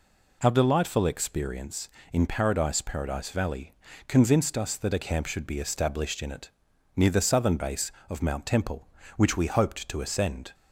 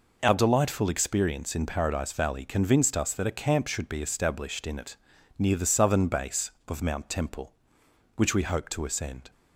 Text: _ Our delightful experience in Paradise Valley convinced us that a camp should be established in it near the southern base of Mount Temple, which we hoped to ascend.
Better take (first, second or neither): second